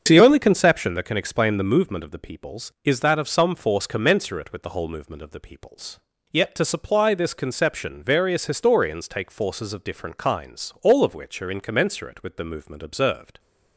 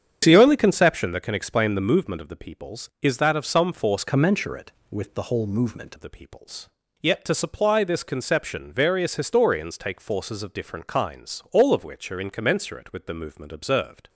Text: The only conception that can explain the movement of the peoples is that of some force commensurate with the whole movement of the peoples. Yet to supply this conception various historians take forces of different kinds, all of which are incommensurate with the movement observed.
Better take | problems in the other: first | starts louder than the rest; strong; until 1.2 s; 8 dB; strong in the first // changes voice from "commensurate" to "movement"; from 4.0 to 5.9 s; 1.9 s long

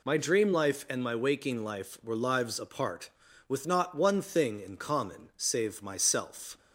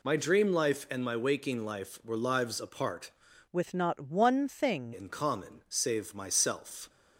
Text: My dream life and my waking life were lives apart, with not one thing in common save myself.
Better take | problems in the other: first | changes voice from "with" to "thing"; from 3.5 to 4.9 s; 1.4 s long

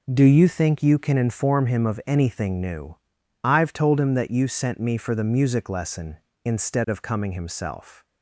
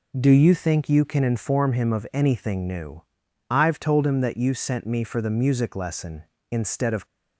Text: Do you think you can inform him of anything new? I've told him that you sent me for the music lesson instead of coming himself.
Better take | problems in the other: first | stops before "coming himself"; at 7.0 s

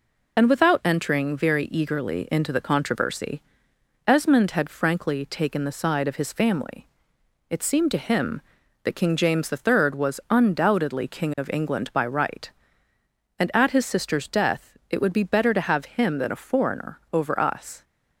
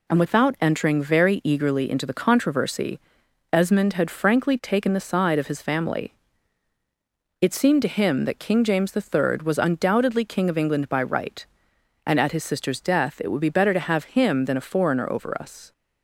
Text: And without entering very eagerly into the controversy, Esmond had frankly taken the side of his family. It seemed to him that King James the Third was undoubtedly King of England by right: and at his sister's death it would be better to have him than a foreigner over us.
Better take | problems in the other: second | loses the start of "And"; at 0.3 s; 30 ms

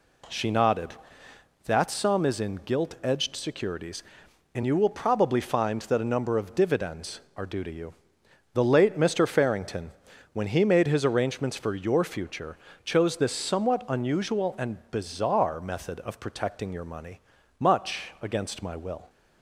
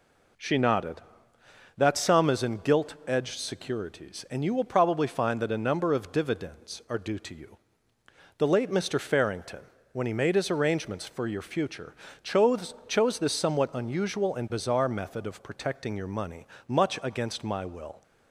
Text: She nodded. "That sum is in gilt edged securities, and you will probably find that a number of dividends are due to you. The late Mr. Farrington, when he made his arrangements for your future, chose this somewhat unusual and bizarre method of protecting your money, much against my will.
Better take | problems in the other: first | says "chose" twice; at 12.8 s

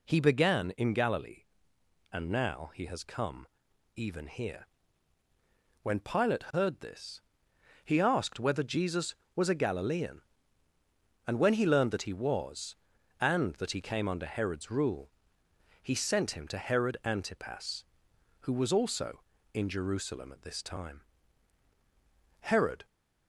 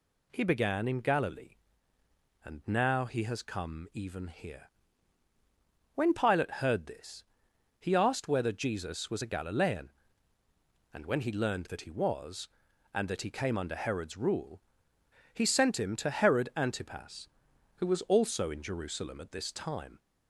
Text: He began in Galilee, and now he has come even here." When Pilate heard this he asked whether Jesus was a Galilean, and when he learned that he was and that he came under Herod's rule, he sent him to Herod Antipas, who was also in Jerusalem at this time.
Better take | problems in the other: second | pauses between "come" and "even"; noticeable; at 3.4 s; 0.48 s long // pauses between "this" and "he"; noticeable; at 7.1 s; 0.64 s long; noticeable in the second // goes on to say "Herod"; slight; from 22.3 s on; 0.48 s long

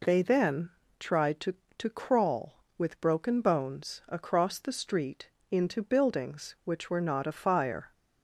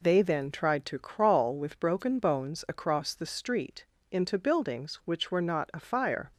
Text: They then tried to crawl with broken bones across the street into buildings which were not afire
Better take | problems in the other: second | pauses between "then" and "tried"; slight; at 0.6 s; 0.30 s long // says "to" twice; at 1.7 s // pauses between "street" and "into"; slight; at 5.2 s; 0.20 s long; slight in the second

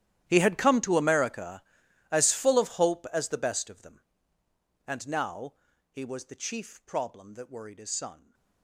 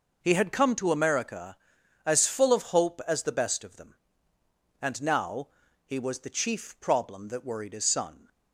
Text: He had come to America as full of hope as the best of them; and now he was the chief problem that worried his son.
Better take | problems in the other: second | gets quieter; strong; throughout; 21 dB // pauses between "now" and "he"; slight; at 5.5 s; 0.36 s long; slight in the second

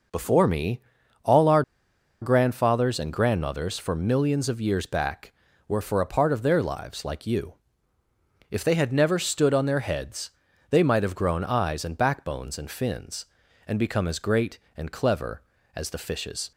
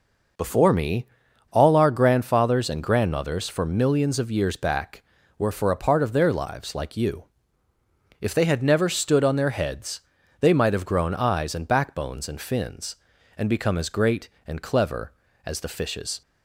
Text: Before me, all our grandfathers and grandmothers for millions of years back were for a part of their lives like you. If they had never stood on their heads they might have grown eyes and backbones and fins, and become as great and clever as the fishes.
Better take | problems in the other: second | pauses between "our" and "grandfathers"; noticeable; at 1.6 s; 0.60 s long // pauses between "heads" and "they"; at 10.3 s; 0.38 s long; also in the second

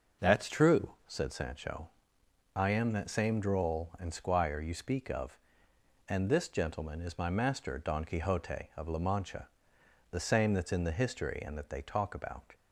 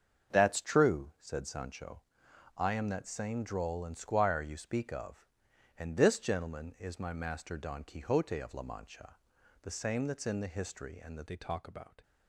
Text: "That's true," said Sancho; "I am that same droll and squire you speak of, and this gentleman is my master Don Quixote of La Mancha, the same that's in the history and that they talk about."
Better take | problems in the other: first | starts louder than the rest; until 1.4 s; 7 dB // changes voice at "they"; from 11.2 s on; 0.8 s long

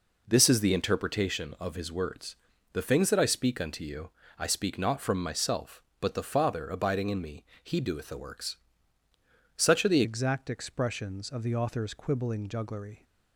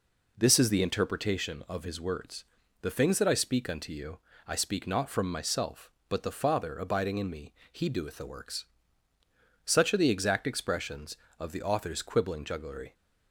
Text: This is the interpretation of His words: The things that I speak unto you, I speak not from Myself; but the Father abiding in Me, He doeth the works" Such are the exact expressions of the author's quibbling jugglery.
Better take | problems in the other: second | pauses between "works" and "Such"; at 8.5 s; 1.0 s long; also in the second // changes voice at "exact"; from 10.0 s on; 3.0 s long

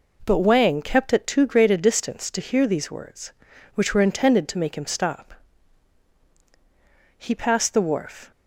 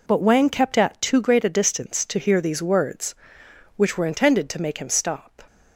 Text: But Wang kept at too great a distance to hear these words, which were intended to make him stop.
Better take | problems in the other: second | goes on to say "He passed the wharf"; noticeable; from 7.1 s on; 1.1 s long

